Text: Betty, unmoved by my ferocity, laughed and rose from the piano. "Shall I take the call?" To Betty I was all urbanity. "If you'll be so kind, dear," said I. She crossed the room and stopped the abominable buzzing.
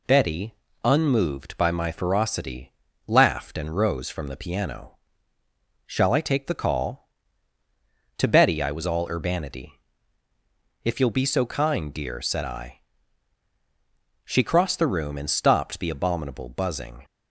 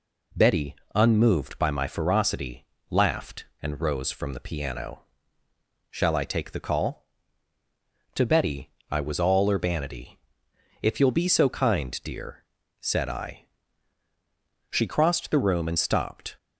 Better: first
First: none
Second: pauses between "Betty" and "I"; slight; at 8.7 s; 0.20 s long // stops before "the abominable buzzing"; at 16.3 s

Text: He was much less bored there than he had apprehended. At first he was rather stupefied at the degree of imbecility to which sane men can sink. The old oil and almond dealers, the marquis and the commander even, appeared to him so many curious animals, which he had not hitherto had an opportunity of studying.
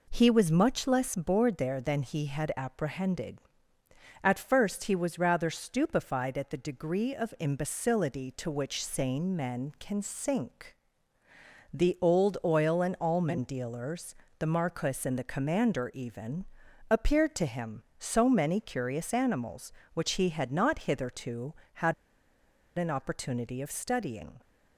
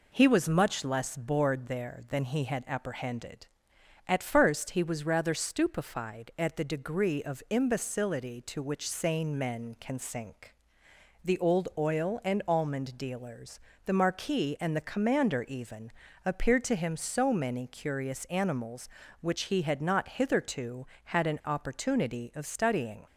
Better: second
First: pauses between "had" and "an"; noticeable; at 21.9 s; 0.83 s long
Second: none

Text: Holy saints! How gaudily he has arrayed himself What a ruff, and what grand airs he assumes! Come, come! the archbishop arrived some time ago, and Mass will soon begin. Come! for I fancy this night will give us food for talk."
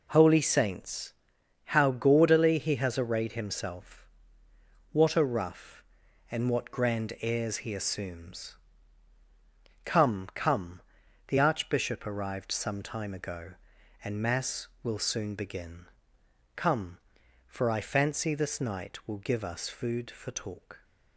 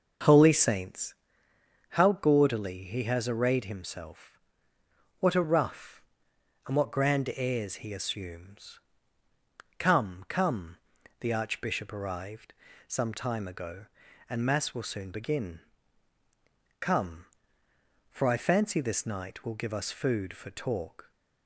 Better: first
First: pauses between "himself" and "What"; noticeable; at 4.0 s; 0.86 s long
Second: starts louder than the rest; noticeable; until 1.5 s; 5.5 dB // pauses between "himself" and "What"; noticeable; at 4.3 s; 0.80 s long // pauses between "arrived" and "some"; slight; at 12.5 s; 0.34 s long

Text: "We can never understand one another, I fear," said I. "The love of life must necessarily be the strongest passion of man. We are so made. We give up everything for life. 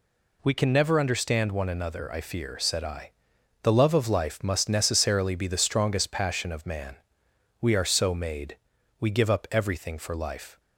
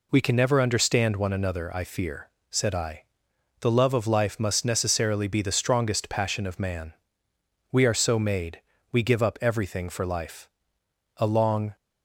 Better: first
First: none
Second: goes on to say "A long"; from 11.1 s on; 0.58 s long

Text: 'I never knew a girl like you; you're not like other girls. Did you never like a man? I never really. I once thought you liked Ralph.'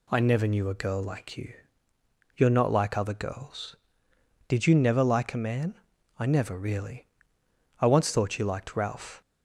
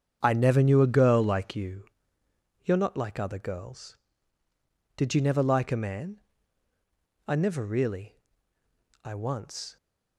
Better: first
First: none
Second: starts louder than the rest; strong; until 1.2 s; 8 dB // stops before "thought you liked Ralph"; at 9.7 s

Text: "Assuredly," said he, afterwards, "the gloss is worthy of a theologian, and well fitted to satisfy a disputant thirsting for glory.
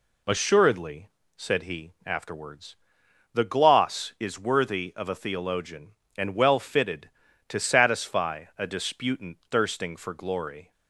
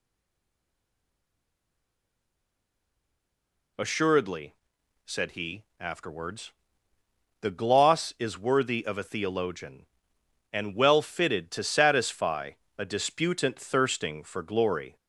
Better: first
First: none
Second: stays silent before the first word; strong; until 3.7 s; 3.7 s long // pauses between "satisfy" and "a"; slight; at 12.5 s; 0.26 s long

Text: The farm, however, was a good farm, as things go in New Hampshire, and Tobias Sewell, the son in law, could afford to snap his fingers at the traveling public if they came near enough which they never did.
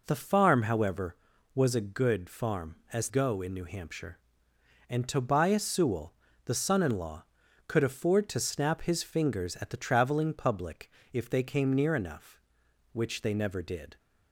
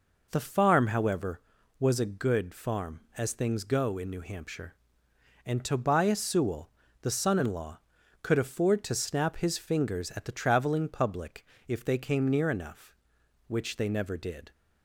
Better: second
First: skips "things"; at 3.0 s // pauses between "public" and "if"; slight; at 10.8 s; 0.24 s long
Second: pauses between "public" and "if"; slight; at 11.4 s; 0.24 s long

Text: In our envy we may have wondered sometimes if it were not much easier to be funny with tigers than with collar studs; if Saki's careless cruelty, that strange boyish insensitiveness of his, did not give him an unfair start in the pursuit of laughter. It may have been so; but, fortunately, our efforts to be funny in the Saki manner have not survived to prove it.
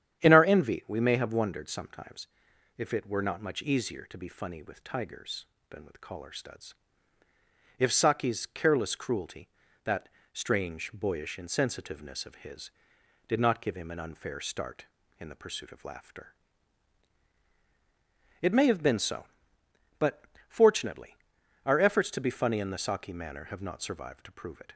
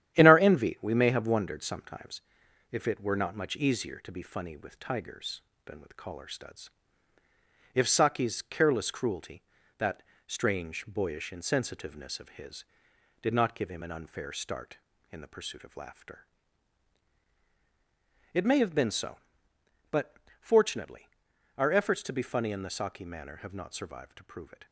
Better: first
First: starts louder than the rest; strong; until 1.2 s; 9.5 dB // pauses between "sometimes" and "if"; noticeable; at 2.2 s; 0.50 s long // pauses between "that" and "strange"; slight; at 10.0 s; 0.24 s long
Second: gets quieter; noticeable; throughout; 5.5 dB // starts louder than the rest; strong; until 1.1 s; 11 dB // pauses between "sometimes" and "if"; noticeable; at 2.2 s; 0.50 s long // pauses between "that" and "strange"; slight; at 10.0 s; 0.24 s long

